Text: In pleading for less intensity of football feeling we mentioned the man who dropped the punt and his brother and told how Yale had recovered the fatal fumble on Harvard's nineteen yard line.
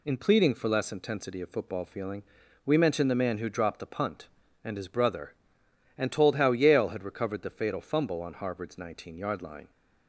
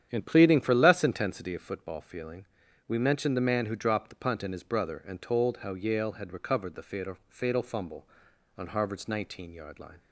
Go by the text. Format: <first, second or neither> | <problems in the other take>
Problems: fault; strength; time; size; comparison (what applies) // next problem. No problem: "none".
first | starts louder than the rest; strong; until 1.1 s; 9.5 dB // pauses between "feeling" and "we"; at 2.4 s; 0.42 s long; also in the first // says "fatal" twice; at 7.2 s